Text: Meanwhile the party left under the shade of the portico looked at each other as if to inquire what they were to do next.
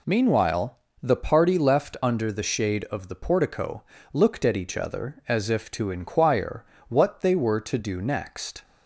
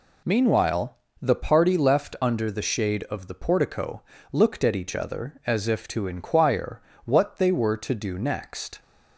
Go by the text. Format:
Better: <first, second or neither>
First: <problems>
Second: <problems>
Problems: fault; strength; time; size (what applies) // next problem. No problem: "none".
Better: neither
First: pauses between "Meanwhile" and "the"; slight; at 0.7 s; 0.24 s long // pauses between "portico" and "looked"; slight; at 3.8 s; 0.30 s long // pauses between "inquire" and "what"; slight; at 6.6 s; 0.24 s long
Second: pauses between "Meanwhile" and "the"; slight; at 0.9 s; 0.24 s long // pauses between "portico" and "looked"; slight; at 4.0 s; 0.30 s long // pauses between "inquire" and "what"; slight; at 6.8 s; 0.24 s long